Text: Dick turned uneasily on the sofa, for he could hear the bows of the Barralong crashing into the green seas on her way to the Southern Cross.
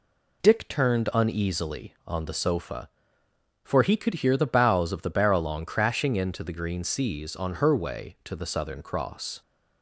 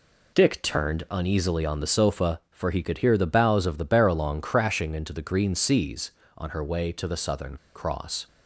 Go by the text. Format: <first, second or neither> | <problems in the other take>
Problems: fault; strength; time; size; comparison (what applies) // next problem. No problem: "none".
first | pauses between "Southern" and "Cross"; slight; at 7.5 s; 0.19 s long